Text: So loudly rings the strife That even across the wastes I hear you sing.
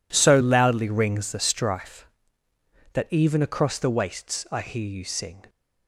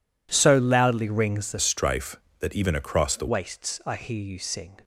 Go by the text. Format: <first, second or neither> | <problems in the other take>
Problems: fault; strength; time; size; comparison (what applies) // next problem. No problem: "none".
first | changes voice from "strife" to "the"; from 1.6 to 3.2 s; 1.6 s long